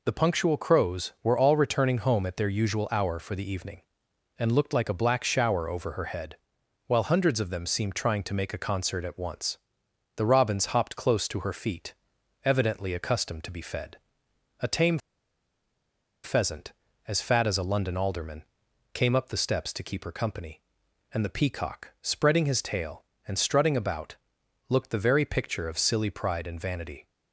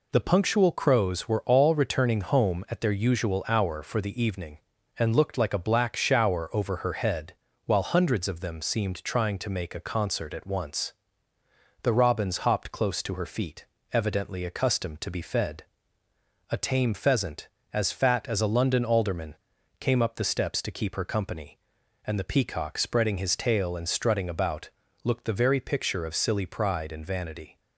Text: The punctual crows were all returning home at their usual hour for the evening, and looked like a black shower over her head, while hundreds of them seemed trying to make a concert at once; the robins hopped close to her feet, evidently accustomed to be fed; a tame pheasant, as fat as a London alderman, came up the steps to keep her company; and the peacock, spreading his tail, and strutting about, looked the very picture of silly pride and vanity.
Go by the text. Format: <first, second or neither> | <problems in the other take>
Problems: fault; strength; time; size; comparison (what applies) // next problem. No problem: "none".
second | pauses between "tame" and "pheasant"; strong; at 14.9 s; 1.2 s long